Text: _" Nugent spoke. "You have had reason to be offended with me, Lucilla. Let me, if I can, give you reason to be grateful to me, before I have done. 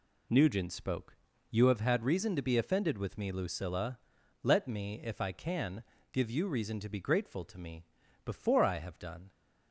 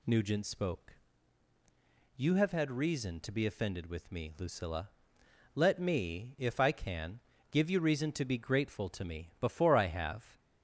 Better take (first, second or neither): first